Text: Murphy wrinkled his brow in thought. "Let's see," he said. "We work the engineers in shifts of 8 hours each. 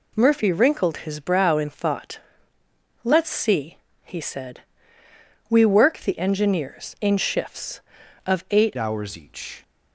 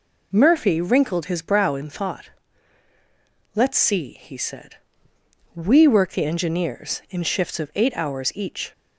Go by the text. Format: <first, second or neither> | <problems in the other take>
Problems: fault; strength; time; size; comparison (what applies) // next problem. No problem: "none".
second | changes voice at "hours"; from 8.7 s on; 0.9 s long